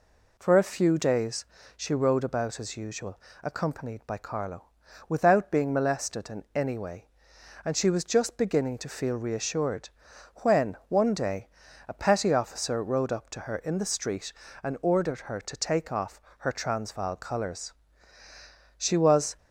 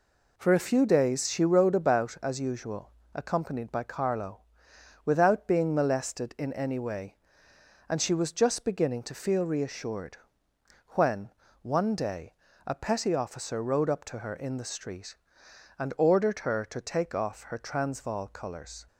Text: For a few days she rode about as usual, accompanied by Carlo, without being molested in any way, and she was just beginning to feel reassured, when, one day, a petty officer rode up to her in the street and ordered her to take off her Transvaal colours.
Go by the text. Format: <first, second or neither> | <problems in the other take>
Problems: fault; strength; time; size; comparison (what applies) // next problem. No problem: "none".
second | pauses between "days" and "she"; slight; at 1.4 s; 0.30 s long // pauses between "off" and "her"; slight; at 16.1 s; 0.20 s long // goes on to say "She was"; from 18.7 s on; 0.60 s long